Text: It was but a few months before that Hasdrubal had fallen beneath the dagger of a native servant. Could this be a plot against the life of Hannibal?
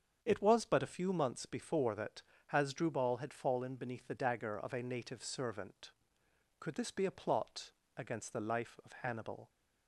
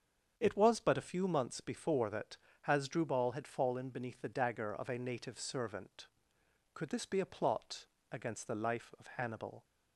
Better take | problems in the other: neither | starts louder than the rest; strong; the same in both // pauses between "that" and "Hasdrubal"; slight; the same in both // pauses between "plot" and "against"; slight; the same in both

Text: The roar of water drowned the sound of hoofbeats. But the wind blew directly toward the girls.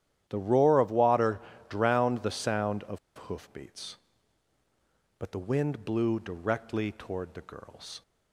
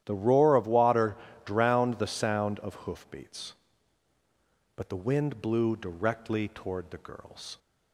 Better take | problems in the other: second | starts louder than the rest; strong; until 1.2 s; 11.5 dB; strong in the second // pauses between "water" and "drowned"; slight; at 1.3 s; 0.30 s long; slight in the second // pauses between "of" and "hoofbeats"; slight; at 2.9 s; 0.19 s long

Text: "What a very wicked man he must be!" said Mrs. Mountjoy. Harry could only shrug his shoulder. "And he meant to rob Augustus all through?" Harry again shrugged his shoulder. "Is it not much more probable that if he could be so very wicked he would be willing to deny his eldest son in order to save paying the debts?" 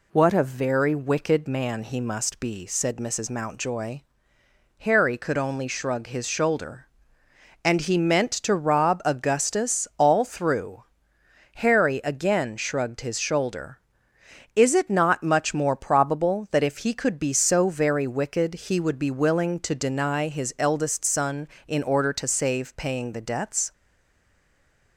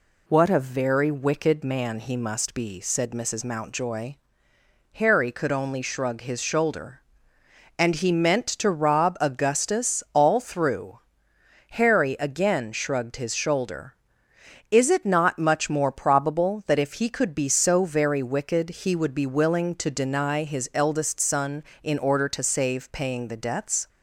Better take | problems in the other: second | stays silent after the last word; noticeable; from 23.7 s on; 1.2 s long

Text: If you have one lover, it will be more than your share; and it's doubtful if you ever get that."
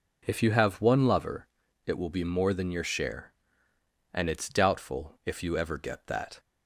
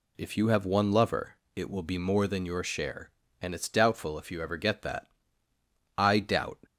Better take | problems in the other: first | goes on to say "I doubt"; from 5.9 s on; 0.60 s long

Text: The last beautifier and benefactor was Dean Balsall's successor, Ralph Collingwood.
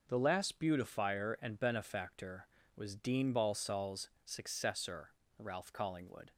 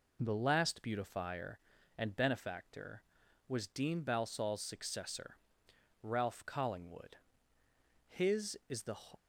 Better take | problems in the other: first | goes on to say "His is the"; noticeable; from 8.0 s on; 0.92 s long

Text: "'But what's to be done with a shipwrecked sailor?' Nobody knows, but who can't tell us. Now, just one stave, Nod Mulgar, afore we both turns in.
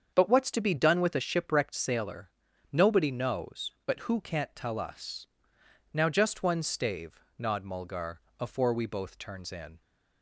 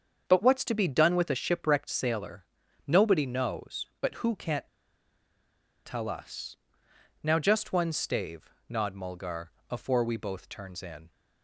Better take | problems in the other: first | starts louder than the rest; strong; until 1.2 s; 7 dB; strong in the first // pauses between "can't" and "tell"; at 4.6 s; 1.1 s long

